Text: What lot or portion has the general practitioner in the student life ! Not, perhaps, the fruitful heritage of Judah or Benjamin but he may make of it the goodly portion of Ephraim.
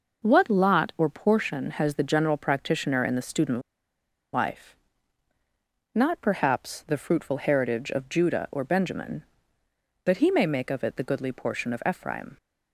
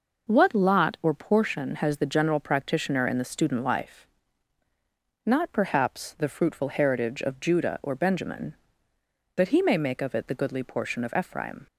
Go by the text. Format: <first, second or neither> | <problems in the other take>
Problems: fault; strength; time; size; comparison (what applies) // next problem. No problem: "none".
second | pauses between "student" and "life"; noticeable; at 3.5 s; 0.74 s long